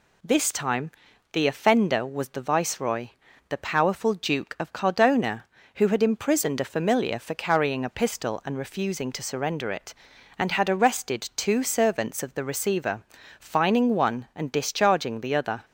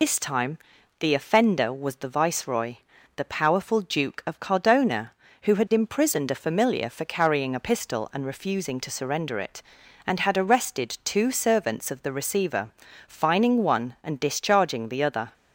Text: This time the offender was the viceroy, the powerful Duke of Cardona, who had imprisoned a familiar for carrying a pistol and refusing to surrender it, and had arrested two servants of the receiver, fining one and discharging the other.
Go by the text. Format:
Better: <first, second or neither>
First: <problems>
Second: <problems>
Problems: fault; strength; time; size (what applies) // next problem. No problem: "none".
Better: first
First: pauses between "time" and "the"; at 0.9 s; 0.42 s long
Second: loses the start of "This"; at 0.0 s; 115 ms // pauses between "time" and "the"; at 0.5 s; 0.42 s long